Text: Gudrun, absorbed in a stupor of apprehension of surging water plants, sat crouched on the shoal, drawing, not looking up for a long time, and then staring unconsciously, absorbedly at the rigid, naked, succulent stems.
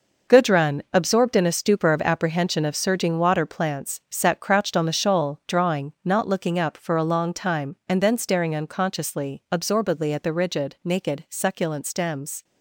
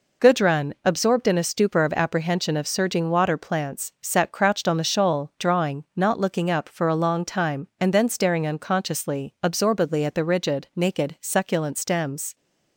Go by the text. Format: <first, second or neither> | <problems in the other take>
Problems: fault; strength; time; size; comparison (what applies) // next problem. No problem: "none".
second | gets quieter; strong; throughout; 10 dB